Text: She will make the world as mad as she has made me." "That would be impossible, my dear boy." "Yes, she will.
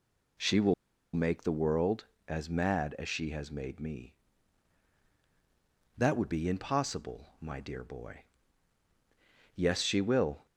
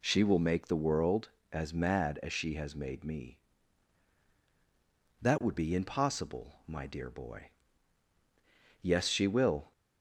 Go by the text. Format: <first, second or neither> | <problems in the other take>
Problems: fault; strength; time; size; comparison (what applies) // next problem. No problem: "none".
second | pauses between "will" and "make"; at 0.7 s; 0.41 s long